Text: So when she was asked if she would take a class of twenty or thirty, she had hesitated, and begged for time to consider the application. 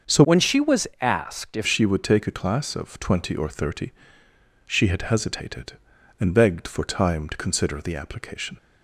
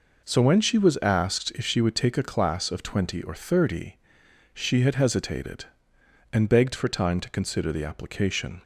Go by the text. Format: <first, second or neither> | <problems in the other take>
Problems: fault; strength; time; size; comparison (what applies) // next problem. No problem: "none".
second | starts louder than the rest; until 1.2 s; 6.5 dB // changes voice from "when" to "if"; from 0.2 to 1.6 s; 1.4 s long